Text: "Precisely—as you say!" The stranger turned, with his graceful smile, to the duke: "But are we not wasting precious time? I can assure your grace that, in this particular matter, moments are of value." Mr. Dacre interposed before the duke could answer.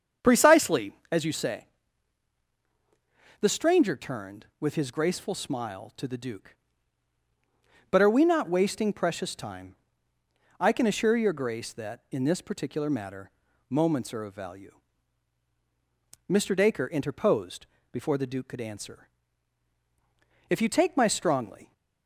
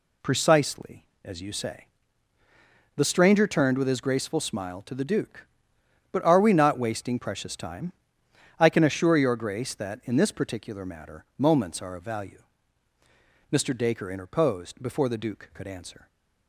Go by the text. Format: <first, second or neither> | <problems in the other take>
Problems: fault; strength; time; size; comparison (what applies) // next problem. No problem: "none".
second | starts louder than the rest; strong; until 1.3 s; 7.5 dB // pauses between "interposed" and "before"; slight; at 17.6 s; 0.26 s long // goes on to say "If you take my strongly"; noticeable; from 20.5 s on; 1.2 s long